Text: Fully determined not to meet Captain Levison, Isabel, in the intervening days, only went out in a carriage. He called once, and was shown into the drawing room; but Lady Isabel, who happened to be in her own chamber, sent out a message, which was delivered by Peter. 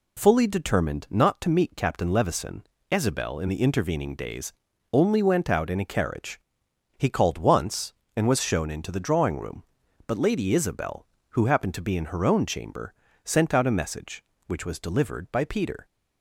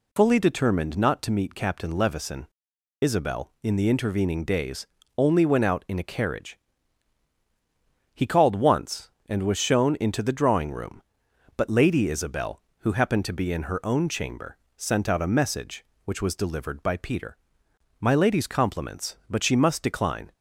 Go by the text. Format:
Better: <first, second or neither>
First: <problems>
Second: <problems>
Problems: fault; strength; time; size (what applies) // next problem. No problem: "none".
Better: first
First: none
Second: goes on to say "My lady's compliments but she must decline"; strong; from 18.0 s on; 2.3 s long